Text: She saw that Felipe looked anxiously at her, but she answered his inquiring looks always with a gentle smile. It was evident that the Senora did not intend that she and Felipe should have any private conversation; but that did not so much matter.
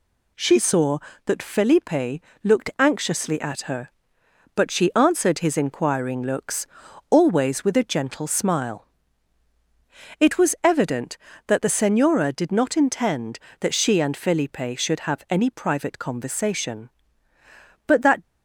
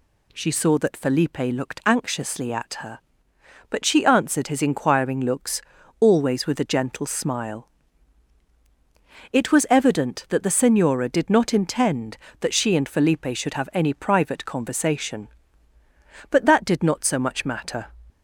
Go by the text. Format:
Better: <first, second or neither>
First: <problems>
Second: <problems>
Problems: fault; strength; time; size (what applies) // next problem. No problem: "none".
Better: second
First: pauses between "Felipe" and "looked"; slight; at 2.2 s; 0.22 s long // pauses between "looks" and "always"; at 6.6 s; 0.42 s long // stops before "did not so much matter"; at 18.2 s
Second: pauses between "looks" and "always"; at 5.6 s; 0.38 s long